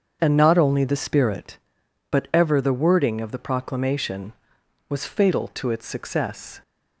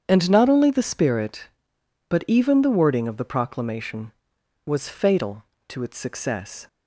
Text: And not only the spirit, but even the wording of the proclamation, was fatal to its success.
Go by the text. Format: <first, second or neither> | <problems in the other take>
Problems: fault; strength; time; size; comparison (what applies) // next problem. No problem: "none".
second | starts louder than the rest; until 1.2 s; 7 dB; strong in the second // says "ever" for "even"; at 2.3 s